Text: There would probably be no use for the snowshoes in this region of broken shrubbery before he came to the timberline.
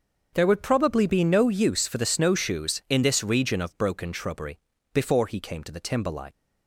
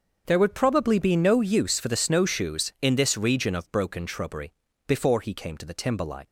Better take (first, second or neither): neither